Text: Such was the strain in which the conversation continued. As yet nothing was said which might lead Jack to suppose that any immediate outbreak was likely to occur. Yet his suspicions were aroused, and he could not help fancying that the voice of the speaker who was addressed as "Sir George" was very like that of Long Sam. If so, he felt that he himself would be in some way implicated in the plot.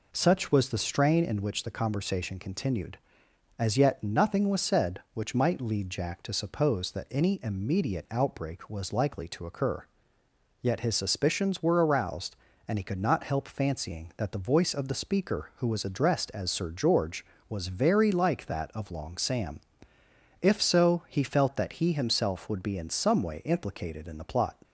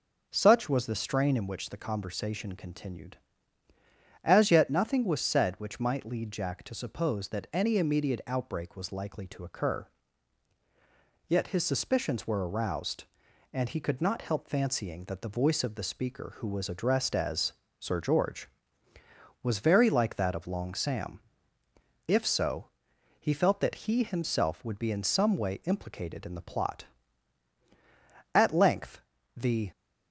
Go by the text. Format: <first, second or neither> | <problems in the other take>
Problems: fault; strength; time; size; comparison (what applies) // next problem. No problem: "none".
first | pauses between "as" and "Sir"; slight; at 17.5 s; 0.26 s long // goes on to say "At length the"; from 28.3 s on; 1.3 s long